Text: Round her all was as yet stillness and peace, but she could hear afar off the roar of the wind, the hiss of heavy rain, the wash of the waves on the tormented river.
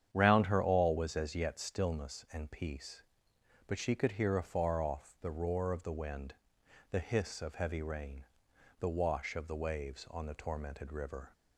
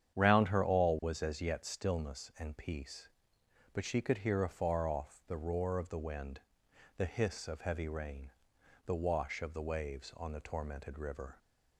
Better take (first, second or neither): neither